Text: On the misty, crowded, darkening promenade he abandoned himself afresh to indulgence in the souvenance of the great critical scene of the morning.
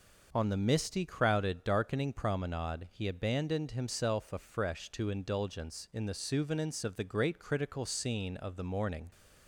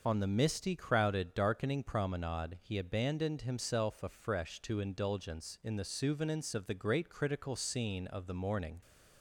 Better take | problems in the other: first | loses the start of "On"; at 0.0 s; 25 ms

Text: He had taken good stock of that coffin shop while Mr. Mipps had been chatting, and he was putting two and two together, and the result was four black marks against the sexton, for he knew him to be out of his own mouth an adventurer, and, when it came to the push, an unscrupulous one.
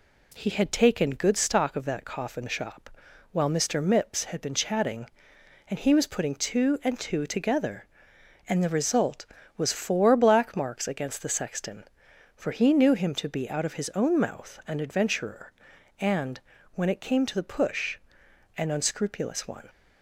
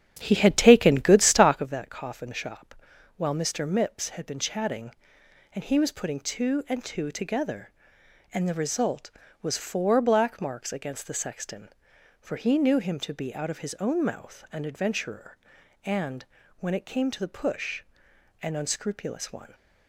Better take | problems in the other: first | starts louder than the rest; strong; until 1.7 s; 9.5 dB // pauses between "shop" and "while"; at 2.7 s; 0.44 s long; also in the first

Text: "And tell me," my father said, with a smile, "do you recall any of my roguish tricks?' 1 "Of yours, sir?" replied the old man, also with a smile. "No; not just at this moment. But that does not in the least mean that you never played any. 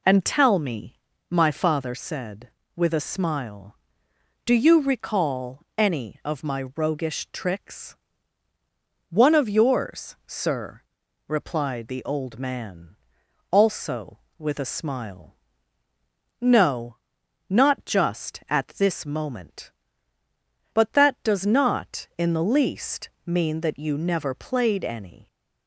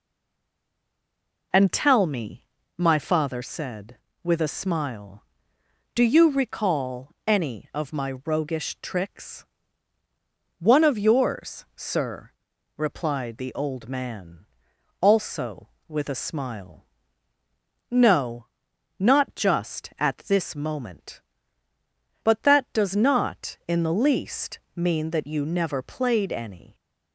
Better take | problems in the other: first | stays silent before the first word; noticeable; until 1.5 s; 1.5 s long // pauses between "recall" and "any"; slight; at 7.1 s; 0.16 s long; slight in the first // pauses between "least" and "mean"; slight; at 24.6 s; 0.16 s long; slight in the first

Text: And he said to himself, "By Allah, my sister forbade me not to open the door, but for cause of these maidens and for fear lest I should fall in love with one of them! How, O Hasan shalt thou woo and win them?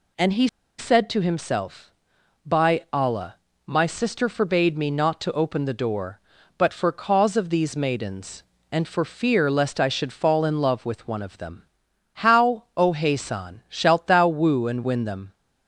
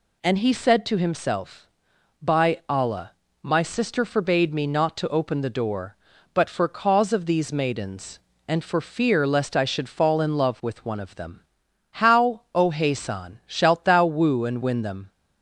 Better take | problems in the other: second | pauses between "he" and "said"; slight; at 0.4 s; 0.32 s long

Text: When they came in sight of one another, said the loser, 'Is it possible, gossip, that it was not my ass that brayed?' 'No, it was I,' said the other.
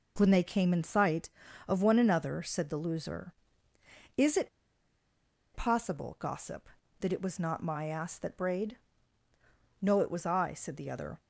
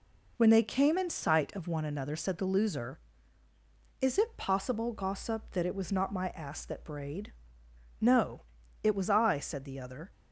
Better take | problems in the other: second | pauses between "it" and "possible"; at 4.4 s; 1.0 s long

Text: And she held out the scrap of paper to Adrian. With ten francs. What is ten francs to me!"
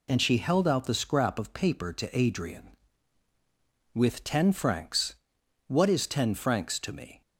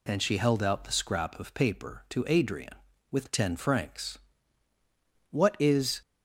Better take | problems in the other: first | stops before "ten francs to me"; at 6.0 s

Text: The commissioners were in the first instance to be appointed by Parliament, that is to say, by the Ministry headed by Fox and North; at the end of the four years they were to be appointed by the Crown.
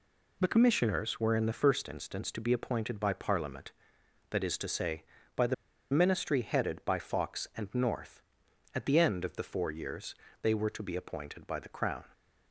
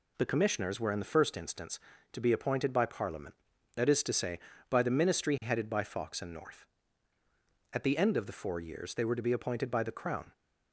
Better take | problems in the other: second | pauses between "the" and "Ministry"; at 5.5 s; 0.37 s long // pauses between "years" and "they"; slight; at 10.1 s; 0.26 s long

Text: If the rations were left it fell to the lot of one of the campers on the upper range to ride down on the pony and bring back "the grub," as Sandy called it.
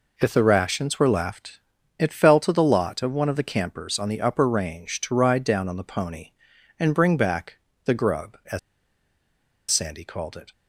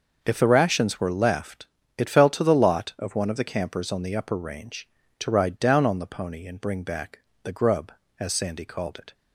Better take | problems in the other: second | pauses between "left" and "it"; at 1.5 s; 0.40 s long; slight in the second // pauses between "back" and "the"; slight; at 7.5 s; 0.28 s long; slight in the second // pauses between "as" and "Sandy"; at 8.5 s; 1.1 s long

